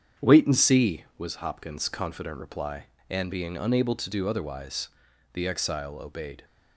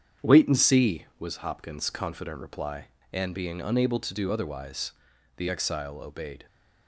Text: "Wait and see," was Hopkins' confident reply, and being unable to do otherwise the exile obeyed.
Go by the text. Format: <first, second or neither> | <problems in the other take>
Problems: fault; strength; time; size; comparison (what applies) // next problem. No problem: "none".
neither | starts louder than the rest; strong; the same in both // pauses between "otherwise" and "the"; the same in both